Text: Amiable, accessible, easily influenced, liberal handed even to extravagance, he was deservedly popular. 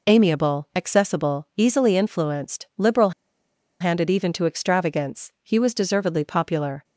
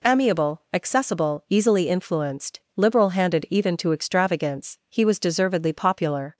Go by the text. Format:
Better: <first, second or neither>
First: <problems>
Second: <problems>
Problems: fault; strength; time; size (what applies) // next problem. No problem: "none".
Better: second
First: pauses between "liberal" and "handed"; noticeable; at 3.1 s; 0.70 s long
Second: none